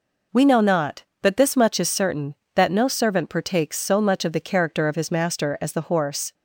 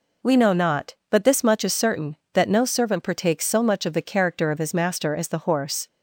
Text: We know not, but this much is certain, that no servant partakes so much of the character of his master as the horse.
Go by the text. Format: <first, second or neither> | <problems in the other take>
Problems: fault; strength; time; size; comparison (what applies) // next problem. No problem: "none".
neither | none